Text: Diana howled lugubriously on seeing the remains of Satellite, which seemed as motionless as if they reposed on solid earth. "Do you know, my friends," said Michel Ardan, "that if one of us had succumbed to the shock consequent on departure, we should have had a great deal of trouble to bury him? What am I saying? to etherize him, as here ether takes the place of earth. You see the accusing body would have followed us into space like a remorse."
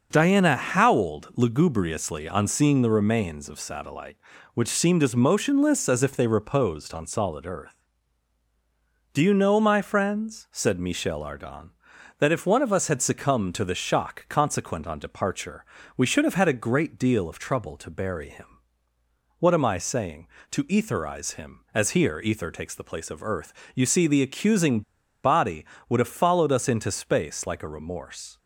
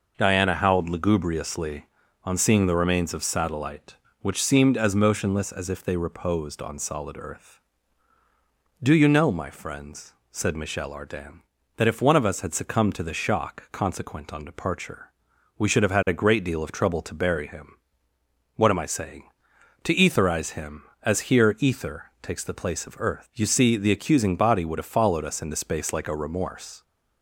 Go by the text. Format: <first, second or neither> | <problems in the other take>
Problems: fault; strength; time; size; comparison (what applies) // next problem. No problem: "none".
second | pauses between "accusing" and "body"; at 24.8 s; 0.42 s long